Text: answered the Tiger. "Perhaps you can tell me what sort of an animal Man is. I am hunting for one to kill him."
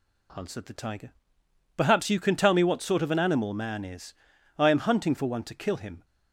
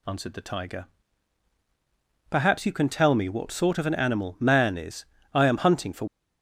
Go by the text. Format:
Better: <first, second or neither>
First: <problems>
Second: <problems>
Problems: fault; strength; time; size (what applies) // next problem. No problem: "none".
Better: first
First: none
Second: stops before "one to kill him"; at 6.0 s